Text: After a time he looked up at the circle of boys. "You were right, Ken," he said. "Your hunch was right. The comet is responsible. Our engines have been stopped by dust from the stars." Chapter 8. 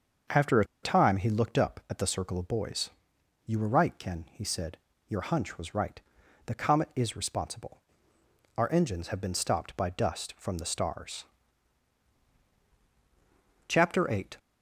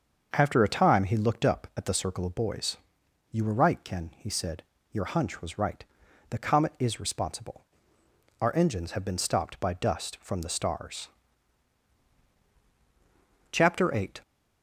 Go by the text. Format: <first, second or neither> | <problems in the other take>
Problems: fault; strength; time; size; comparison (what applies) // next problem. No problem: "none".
second | starts louder than the rest; until 1.4 s; 6.5 dB; also in the second // pauses between "a" and "time"; slight; at 0.6 s; 0.18 s long